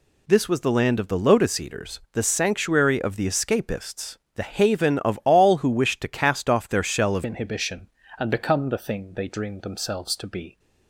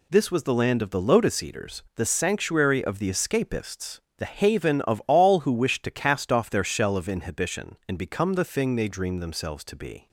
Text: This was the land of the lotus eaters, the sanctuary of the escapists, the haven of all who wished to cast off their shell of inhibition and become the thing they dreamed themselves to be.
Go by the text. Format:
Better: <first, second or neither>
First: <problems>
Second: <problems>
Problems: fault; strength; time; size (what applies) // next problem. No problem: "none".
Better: second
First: changes voice at "inhibition"; from 7.2 s on; 3.3 s long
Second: none